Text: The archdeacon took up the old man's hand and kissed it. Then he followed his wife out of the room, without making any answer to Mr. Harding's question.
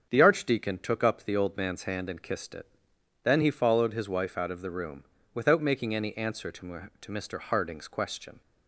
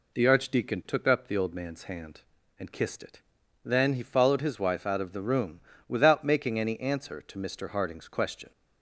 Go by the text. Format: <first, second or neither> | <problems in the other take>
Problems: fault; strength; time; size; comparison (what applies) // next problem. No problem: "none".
second | starts louder than the rest; strong; until 1.1 s; 7.5 dB // says "to" twice; at 7.0 s